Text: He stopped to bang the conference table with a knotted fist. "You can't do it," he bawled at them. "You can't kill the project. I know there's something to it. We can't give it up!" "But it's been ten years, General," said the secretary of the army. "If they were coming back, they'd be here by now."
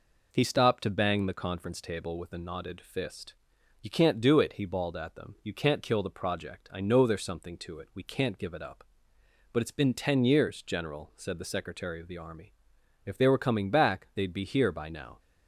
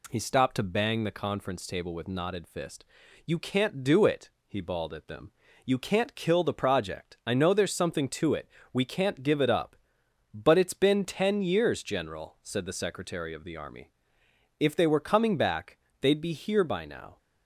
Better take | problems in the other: first | skips "a"; at 2.0 s

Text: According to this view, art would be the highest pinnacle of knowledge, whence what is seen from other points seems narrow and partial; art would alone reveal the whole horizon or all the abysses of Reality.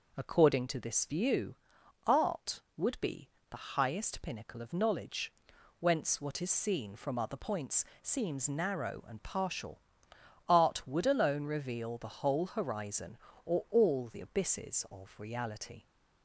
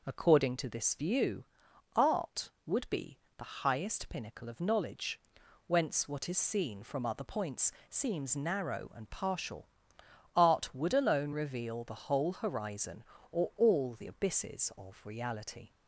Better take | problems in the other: neither | pauses between "be" and "the"; slight; the same in both // pauses between "points" and "seems"; slight; the same in both

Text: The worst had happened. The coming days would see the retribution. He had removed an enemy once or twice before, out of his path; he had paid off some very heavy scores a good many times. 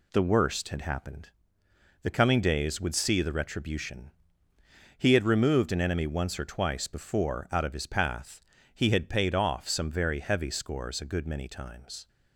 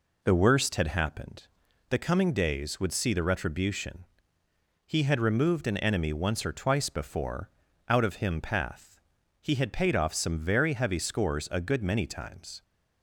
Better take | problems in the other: first | says "him" for "his"; at 8.1 s

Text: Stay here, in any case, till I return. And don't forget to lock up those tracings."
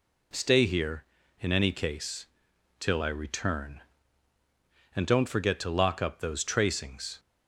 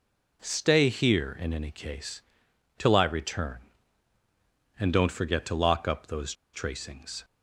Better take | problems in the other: first | pauses between "those" and "tracings"; slight; at 6.3 s; 0.20 s long

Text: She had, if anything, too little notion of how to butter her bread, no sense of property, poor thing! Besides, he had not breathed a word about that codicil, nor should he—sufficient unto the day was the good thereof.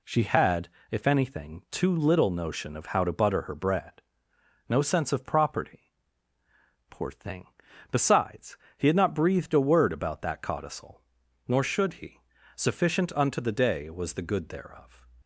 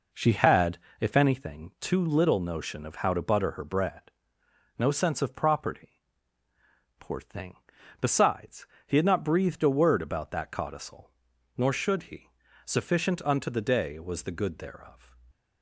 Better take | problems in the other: first | starts louder than the rest; noticeable; until 1.4 s; 4.5 dB

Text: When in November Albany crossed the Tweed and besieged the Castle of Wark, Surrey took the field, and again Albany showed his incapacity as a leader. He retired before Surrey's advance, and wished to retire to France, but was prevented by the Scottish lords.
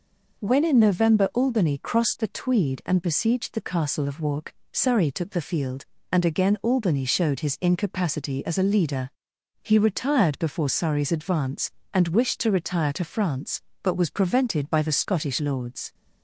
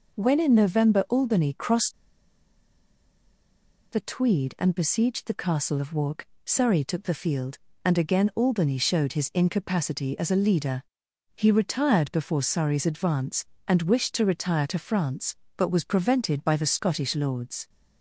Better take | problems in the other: first | pauses between "crossed" and "the"; strong; at 1.9 s; 1.9 s long

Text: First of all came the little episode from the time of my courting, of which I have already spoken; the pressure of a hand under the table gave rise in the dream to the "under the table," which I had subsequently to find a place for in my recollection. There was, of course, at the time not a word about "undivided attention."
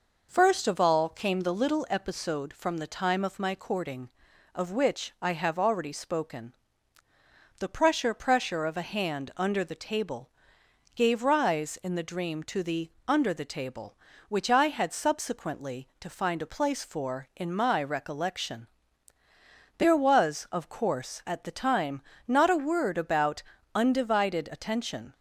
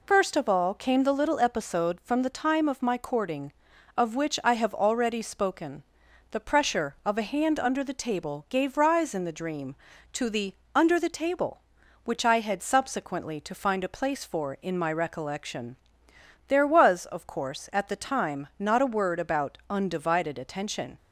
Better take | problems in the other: second | says "pressure" twice; at 8.1 s // pauses between "table" and "gave"; noticeable; at 10.2 s; 0.64 s long // pauses between "the" and "under"; slight; at 12.9 s; 0.16 s long; slight in the second // pauses between "time" and "not"; slight; at 22.0 s; 0.26 s long // pauses between "about" and "undivided"; slight; at 23.4 s; 0.32 s long

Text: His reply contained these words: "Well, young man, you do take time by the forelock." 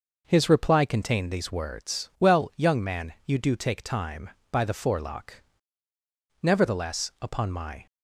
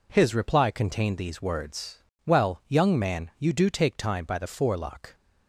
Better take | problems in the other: second | goes on to say "Nevertheless upon my"; from 6.4 s on; 1.4 s long

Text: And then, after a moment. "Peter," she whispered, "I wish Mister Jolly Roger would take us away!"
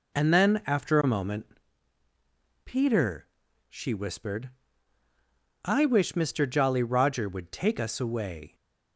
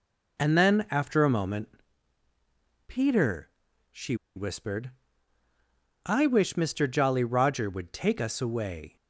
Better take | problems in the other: first | pauses between "she" and "whispered"; slight; at 4.1 s; 0.20 s long

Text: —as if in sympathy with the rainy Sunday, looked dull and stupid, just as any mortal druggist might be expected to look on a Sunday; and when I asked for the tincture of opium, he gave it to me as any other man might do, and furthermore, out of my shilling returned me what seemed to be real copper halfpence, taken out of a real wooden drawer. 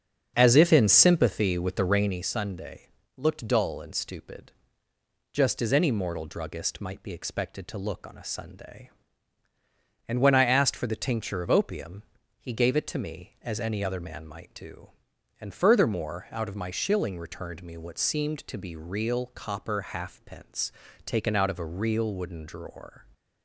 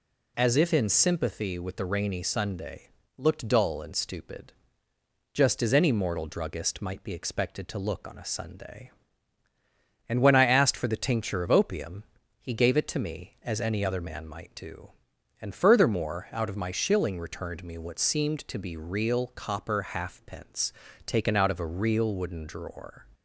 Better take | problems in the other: second | starts louder than the rest; until 2.3 s; 7 dB

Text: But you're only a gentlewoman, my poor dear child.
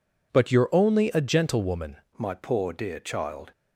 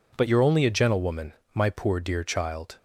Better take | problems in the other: second | changes voice at "my"; from 2.1 s on; 1.4 s long

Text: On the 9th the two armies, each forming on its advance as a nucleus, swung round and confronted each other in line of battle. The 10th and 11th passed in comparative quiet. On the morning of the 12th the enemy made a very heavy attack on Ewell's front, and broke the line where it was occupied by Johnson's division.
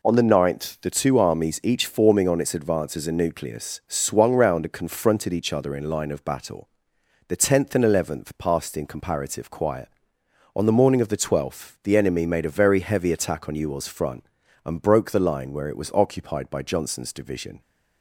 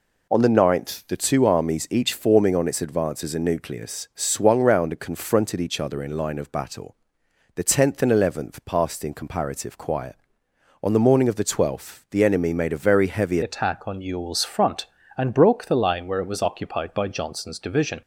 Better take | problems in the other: first | changes voice at "attack"; from 13.4 s on; 4.6 s long

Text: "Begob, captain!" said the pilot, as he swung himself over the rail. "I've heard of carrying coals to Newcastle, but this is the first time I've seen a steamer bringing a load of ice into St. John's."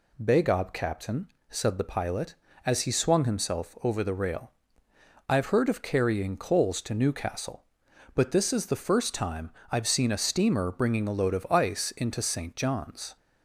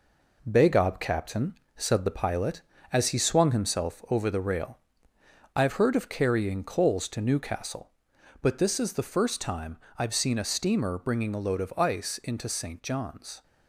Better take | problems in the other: first | gets quieter; noticeable; throughout; 5.5 dB // pauses between "time" and "I've"; slight; at 9.7 s; 0.22 s long; slight in the first

